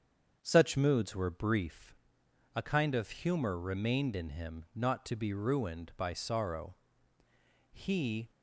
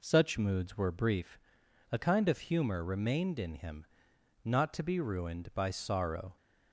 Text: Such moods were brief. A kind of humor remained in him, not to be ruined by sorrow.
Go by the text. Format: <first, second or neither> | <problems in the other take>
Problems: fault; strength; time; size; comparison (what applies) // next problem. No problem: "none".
second | starts louder than the rest; strong; until 1.4 s; 7.5 dB // goes on to say "He"; from 7.7 s on; 0.58 s long